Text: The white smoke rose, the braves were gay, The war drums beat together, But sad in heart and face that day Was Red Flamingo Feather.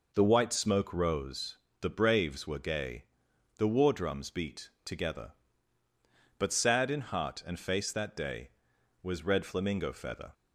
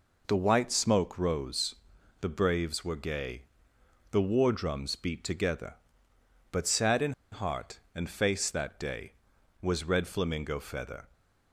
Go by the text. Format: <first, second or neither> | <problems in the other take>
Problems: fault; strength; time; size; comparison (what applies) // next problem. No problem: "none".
first | pauses between "in" and "heart"; slight; at 7.1 s; 0.20 s long